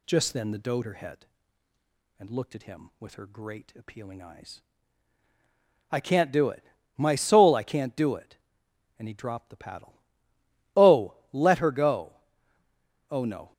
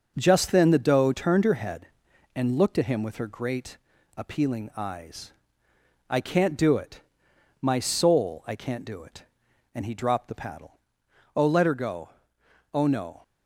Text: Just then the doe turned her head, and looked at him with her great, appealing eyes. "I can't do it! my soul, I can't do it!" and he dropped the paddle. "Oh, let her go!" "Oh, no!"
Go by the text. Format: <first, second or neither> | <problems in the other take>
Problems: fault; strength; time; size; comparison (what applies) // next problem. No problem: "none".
second | skips "turned"; at 0.8 s